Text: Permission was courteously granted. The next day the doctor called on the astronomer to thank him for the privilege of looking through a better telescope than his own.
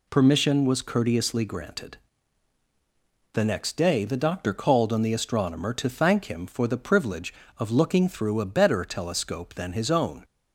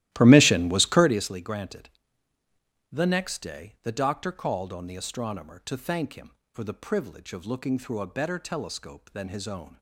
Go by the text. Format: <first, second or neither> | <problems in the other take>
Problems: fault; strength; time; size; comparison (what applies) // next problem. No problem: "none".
first | starts louder than the rest; strong; until 1.3 s; 14.5 dB